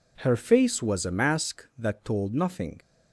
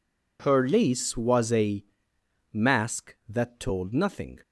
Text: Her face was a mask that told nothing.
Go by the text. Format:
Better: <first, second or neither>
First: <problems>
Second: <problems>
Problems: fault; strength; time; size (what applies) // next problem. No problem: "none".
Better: first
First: none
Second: says "lace" for "face"; at 0.6 s // pauses between "a" and "mask"; noticeable; at 1.8 s; 0.66 s long